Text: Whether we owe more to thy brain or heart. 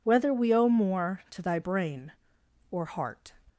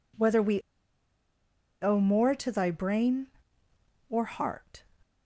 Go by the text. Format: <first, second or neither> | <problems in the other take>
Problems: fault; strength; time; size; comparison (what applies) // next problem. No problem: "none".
first | pauses between "we" and "owe"; at 0.6 s; 1.2 s long